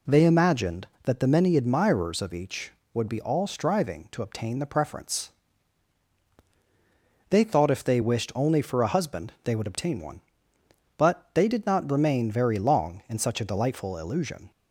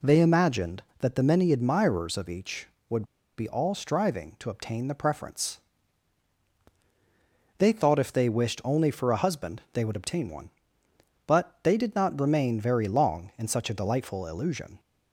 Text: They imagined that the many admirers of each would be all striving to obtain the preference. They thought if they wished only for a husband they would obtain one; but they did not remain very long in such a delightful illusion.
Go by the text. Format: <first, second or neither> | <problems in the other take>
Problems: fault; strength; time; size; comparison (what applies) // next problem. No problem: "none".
first | pauses between "would" and "be"; slight; at 3.0 s; 0.34 s long